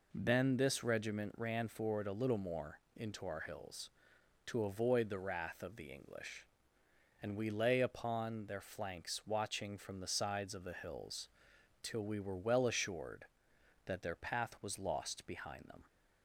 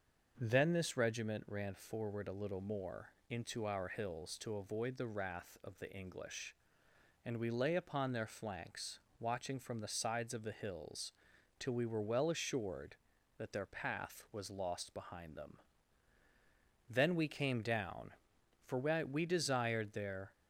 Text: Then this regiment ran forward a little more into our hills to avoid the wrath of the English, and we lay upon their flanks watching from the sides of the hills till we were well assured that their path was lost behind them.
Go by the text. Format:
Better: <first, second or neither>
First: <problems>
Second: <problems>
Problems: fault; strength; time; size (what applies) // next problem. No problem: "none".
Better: first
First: pauses between "more" and "into"; slight; at 2.7 s; 0.18 s long // pauses between "hills" and "till"; noticeable; at 11.2 s; 0.54 s long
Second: starts louder than the rest; until 1.3 s; 6.5 dB // pauses between "more" and "into"; slight; at 3.1 s; 0.18 s long // pauses between "flanks" and "watching"; slight; at 8.9 s; 0.18 s long // pauses between "hills" and "till"; at 11.1 s; 0.44 s long // goes on to say "Then we came down for we desired their"; strong; from 16.8 s on; 3.4 s long